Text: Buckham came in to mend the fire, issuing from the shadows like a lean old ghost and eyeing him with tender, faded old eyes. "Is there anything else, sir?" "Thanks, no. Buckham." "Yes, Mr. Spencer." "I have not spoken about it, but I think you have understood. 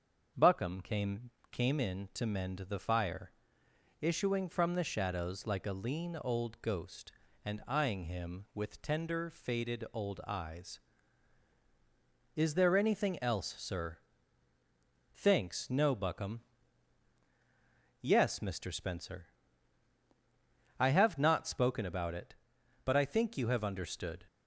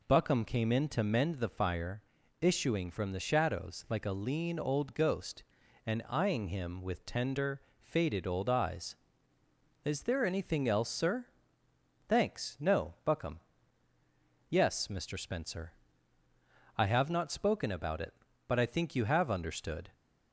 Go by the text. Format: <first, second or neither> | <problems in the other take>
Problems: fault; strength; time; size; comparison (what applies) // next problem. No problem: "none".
second | starts louder than the rest; until 1.5 s; 6.5 dB // says "came" twice; at 1.5 s